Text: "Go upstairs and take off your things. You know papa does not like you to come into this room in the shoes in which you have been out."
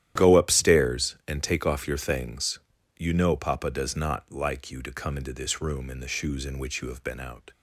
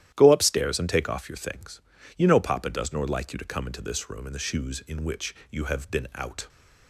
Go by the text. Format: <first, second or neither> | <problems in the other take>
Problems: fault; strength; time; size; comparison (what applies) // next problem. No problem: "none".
first | starts louder than the rest; strong; until 1.1 s; 12 dB; strong in the first // says "nor" for "not"; at 2.9 s // pauses between "which" and "you"; slight; at 5.3 s; 0.16 s long